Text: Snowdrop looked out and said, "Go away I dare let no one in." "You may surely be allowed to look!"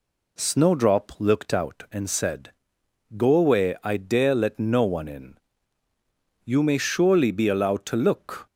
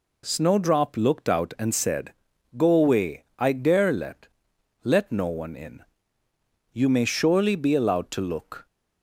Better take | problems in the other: first | says "let" twice; at 4.8 s

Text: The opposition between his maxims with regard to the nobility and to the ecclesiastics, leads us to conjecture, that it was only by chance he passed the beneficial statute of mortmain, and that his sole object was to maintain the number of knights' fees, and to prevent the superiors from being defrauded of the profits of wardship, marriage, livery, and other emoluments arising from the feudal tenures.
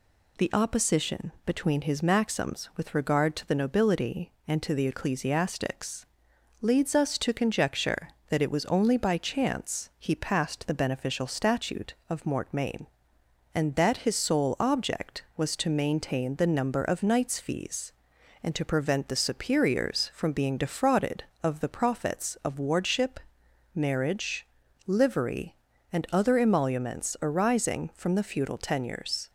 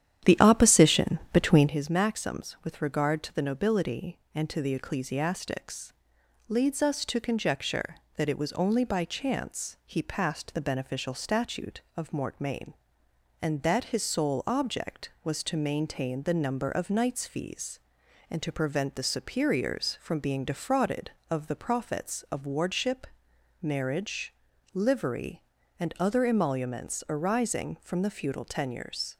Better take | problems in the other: first | starts louder than the rest; strong; until 1.7 s; 10 dB

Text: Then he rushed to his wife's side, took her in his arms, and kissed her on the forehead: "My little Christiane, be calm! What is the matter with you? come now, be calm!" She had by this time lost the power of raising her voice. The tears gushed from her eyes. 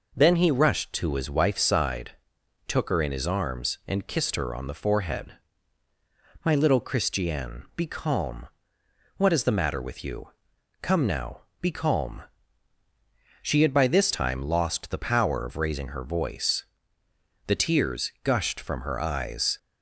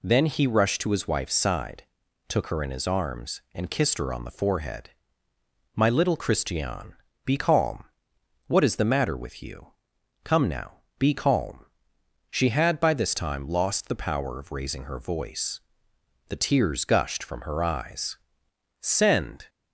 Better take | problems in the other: first | goes on to say "Send"; noticeable; from 18.7 s on; 0.70 s long

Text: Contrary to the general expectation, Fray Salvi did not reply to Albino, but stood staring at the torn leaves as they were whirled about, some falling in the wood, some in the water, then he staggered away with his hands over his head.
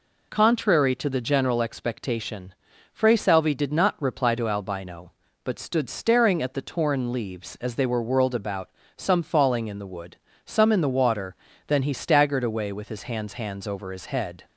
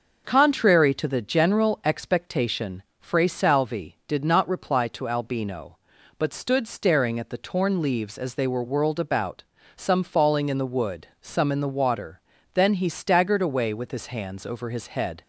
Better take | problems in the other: second | says "hands" twice; at 13.3 s

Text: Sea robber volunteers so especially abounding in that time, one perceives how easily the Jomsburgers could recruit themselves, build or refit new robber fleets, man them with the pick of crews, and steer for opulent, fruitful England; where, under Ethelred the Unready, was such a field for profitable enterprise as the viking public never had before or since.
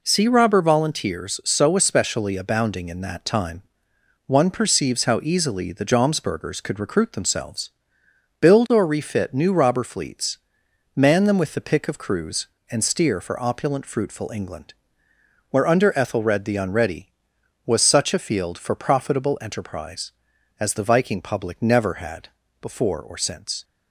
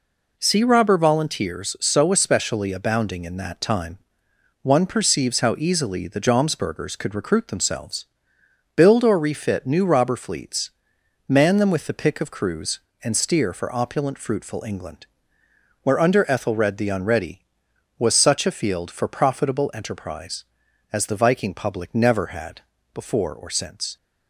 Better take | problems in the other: neither | pauses between "had" and "before"; slight; the same in both

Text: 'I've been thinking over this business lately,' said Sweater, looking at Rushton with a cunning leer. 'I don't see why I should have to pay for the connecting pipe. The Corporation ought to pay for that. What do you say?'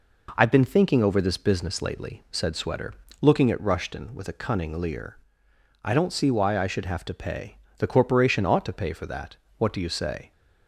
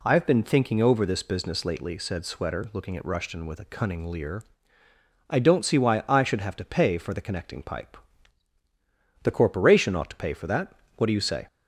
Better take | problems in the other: second | skips "for the connecting pipe"; at 7.6 s

